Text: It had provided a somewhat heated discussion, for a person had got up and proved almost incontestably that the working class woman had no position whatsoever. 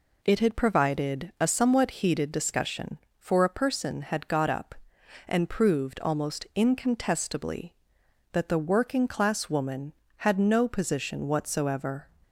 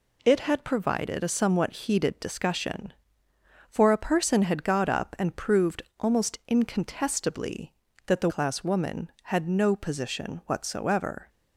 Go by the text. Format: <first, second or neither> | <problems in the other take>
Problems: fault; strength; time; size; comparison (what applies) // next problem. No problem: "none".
first | pauses between "proved" and "almost"; slight; at 5.8 s; 0.16 s long // skips "working"; at 8.2 s